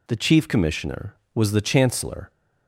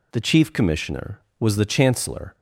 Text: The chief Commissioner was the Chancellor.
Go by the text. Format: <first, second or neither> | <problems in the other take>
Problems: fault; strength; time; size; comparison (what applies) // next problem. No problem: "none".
neither | none